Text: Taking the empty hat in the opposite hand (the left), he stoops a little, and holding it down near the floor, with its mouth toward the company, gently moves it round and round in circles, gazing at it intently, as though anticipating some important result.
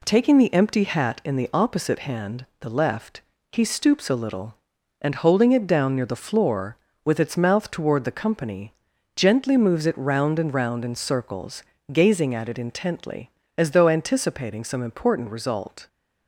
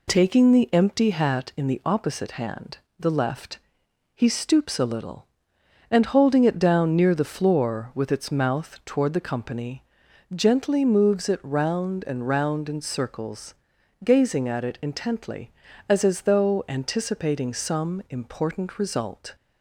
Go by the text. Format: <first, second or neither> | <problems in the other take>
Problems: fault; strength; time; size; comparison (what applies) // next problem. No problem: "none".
first | says "as" twice; at 16.0 s